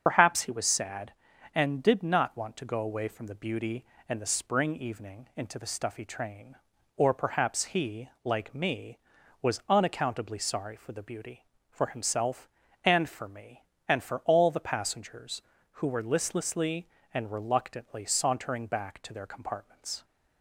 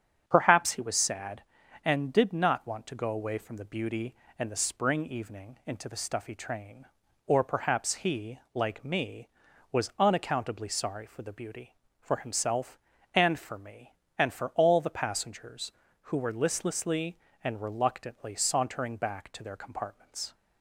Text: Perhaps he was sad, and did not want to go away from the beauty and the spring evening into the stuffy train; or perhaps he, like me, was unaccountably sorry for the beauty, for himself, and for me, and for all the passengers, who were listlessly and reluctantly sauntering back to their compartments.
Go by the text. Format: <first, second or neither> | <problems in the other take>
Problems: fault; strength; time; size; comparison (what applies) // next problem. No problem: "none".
second | loses the start of "Perhaps"; at 0.0 s; 80 ms // starts louder than the rest; until 1.0 s; 7 dB; strong in the second